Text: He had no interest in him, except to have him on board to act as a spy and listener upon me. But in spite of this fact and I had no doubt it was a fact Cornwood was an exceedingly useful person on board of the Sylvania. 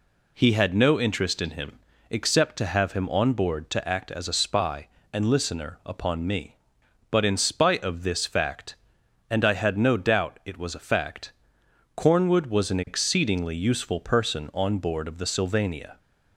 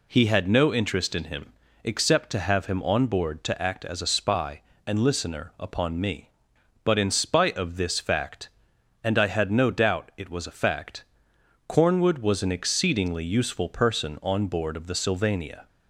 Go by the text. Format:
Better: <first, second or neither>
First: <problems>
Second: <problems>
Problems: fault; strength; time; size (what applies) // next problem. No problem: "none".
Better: neither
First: pauses between "fact" and "Cornwood"; noticeable; at 11.3 s; 0.64 s long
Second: pauses between "fact" and "Cornwood"; noticeable; at 11.0 s; 0.64 s long